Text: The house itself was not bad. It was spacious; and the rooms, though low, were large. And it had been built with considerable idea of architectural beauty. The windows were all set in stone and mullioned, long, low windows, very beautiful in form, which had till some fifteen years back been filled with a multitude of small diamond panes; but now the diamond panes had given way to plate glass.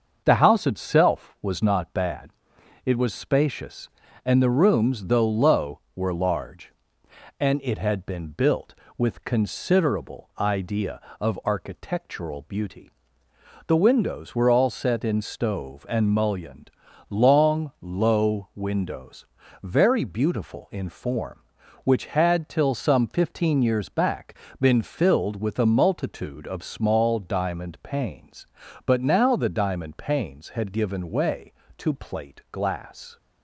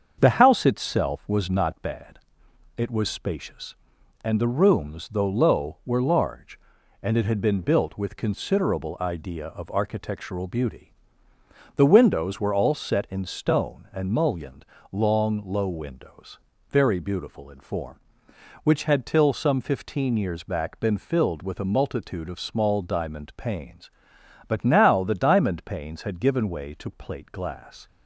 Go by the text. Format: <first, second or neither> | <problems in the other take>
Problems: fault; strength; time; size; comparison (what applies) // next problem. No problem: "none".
second | starts louder than the rest; until 1.2 s; 6.5 dB; also in the second // says "stove" for "stone"; at 15.2 s // pauses between "back" and "been"; slight; at 24.3 s; 0.24 s long